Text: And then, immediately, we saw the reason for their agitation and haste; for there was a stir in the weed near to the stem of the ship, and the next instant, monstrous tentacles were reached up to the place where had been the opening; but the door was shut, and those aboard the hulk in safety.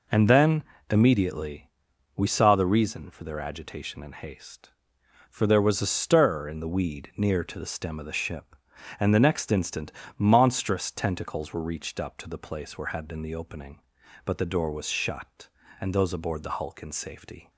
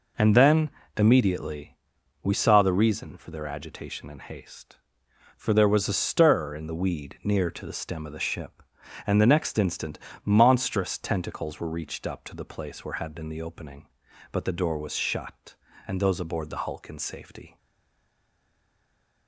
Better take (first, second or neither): first